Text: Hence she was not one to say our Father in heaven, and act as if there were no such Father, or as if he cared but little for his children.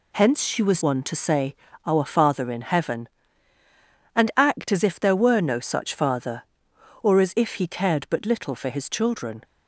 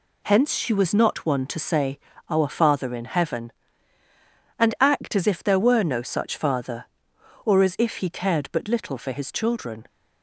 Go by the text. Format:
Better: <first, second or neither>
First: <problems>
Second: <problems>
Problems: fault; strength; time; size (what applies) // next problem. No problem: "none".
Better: second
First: skips "not"; at 0.8 s // pauses between "say" and "our"; slight; at 1.5 s; 0.32 s long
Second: pauses between "say" and "our"; slight; at 1.9 s; 0.32 s long